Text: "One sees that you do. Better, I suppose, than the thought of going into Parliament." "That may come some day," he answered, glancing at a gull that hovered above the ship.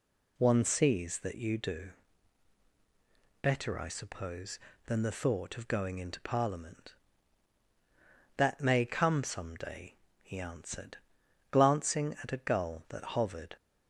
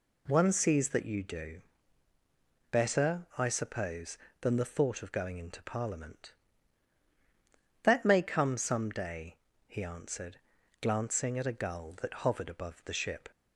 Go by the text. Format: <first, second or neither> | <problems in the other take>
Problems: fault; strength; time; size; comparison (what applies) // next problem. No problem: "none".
second | stops before "above the ship"; at 13.5 s